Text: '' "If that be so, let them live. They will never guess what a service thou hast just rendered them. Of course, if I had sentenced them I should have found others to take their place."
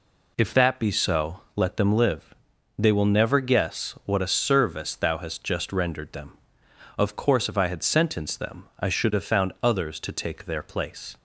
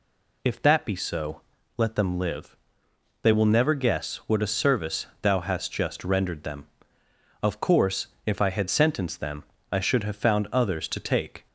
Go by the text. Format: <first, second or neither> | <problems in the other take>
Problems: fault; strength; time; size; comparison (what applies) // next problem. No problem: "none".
first | pauses between "service" and "thou"; slight; at 5.0 s; 0.16 s long // pauses between "them" and "I"; slight; at 9.4 s; 0.28 s long // stops before "their place"; at 11.4 s